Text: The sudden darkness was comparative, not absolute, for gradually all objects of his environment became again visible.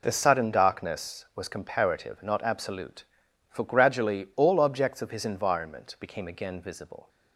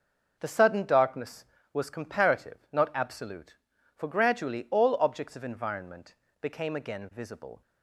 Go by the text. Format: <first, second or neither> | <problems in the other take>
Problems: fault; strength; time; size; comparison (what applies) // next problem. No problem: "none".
first | starts louder than the rest; noticeable; until 1.4 s; 6 dB // skips "his"; at 5.4 s // pauses between "environment" and "became"; slight; at 6.1 s; 0.26 s long